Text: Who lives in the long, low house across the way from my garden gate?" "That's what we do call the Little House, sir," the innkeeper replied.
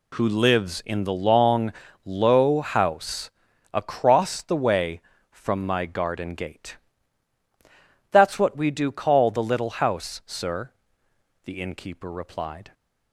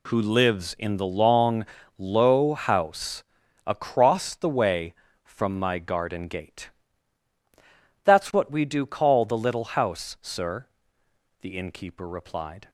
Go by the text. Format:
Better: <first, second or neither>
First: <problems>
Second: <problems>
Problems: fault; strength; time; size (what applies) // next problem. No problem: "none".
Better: neither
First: pauses between "house" and "across"; at 3.3 s; 0.42 s long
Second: pauses between "house" and "across"; at 3.2 s; 0.42 s long